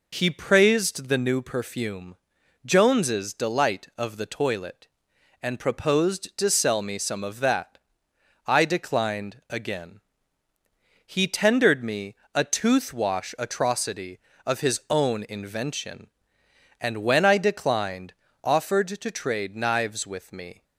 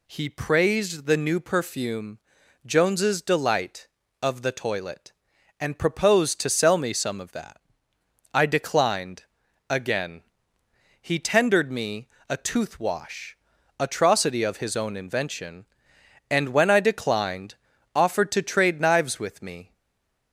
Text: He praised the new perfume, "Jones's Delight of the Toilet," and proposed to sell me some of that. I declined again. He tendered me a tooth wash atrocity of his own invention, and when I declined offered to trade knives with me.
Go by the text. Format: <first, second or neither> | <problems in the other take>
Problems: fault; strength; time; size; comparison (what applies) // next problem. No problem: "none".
first | pauses between "declined" and "again"; at 9.2 s; 0.44 s long // pauses between "me" and "a"; slight; at 12.0 s; 0.22 s long; slight in the first // pauses between "wash" and "atrocity"; at 13.3 s; 0.42 s long // pauses between "declined" and "offered"; at 17.5 s; 0.40 s long; slight in the first // stays silent after the last word; slight; from 19.7 s on; 0.6 s long